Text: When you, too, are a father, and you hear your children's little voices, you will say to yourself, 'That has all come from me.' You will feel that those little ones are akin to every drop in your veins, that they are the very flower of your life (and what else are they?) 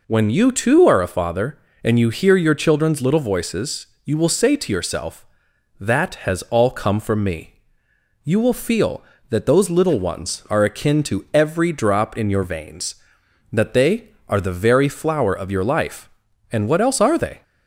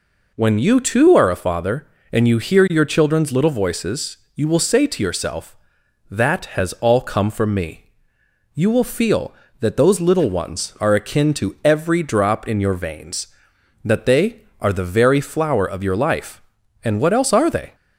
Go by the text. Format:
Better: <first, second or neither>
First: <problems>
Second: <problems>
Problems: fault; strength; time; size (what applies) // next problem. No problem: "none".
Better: neither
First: none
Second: none